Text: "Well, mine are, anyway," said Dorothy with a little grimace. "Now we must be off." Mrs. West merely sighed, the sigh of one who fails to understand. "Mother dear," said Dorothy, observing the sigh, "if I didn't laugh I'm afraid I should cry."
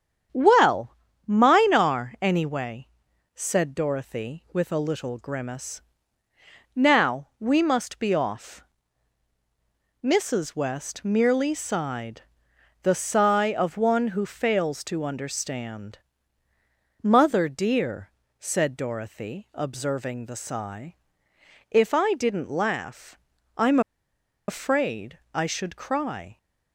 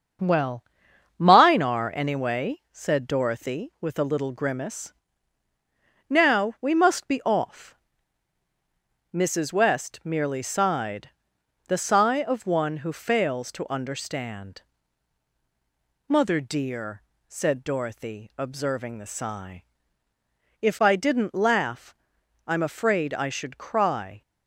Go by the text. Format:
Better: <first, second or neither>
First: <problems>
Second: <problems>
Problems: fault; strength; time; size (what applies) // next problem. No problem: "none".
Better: second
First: starts louder than the rest; strong; until 1.6 s; 8 dB // pauses between "laugh" and "I'm"; at 23.1 s; 0.40 s long // pauses between "I'm" and "afraid"; noticeable; at 23.7 s; 0.68 s long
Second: starts louder than the rest; until 1.7 s; 7 dB // pauses between "laugh" and "I'm"; noticeable; at 21.9 s; 0.50 s long